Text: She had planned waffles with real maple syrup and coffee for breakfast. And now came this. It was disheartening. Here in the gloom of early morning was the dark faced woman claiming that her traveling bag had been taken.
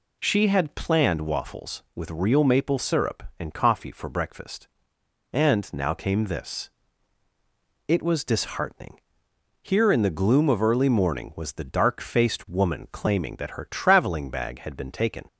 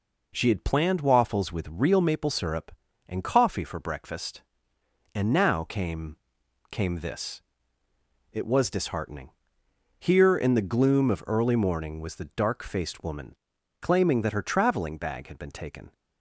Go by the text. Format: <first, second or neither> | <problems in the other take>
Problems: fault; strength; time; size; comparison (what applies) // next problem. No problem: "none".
first | says "came" twice; at 6.7 s // pauses between "woman" and "claiming"; at 13.3 s; 0.44 s long